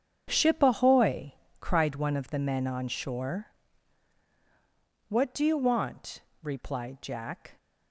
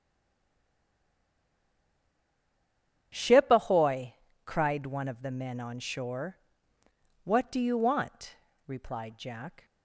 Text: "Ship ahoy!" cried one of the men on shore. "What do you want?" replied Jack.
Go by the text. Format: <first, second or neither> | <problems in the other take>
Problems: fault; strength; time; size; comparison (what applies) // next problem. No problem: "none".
first | stays silent before the first word; strong; until 3.1 s; 3.1 s long // starts louder than the rest; strong; until 4.4 s; 8.5 dB; strong in the first